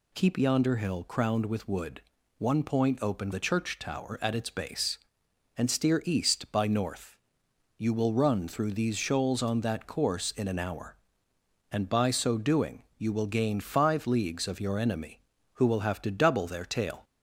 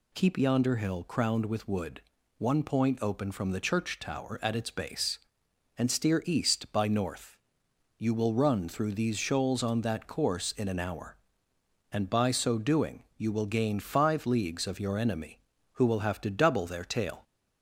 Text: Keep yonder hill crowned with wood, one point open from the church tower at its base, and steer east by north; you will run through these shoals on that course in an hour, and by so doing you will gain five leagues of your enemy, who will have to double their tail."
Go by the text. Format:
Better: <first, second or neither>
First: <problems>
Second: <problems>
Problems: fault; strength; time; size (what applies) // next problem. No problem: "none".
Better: second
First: skips "from"; at 3.3 s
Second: none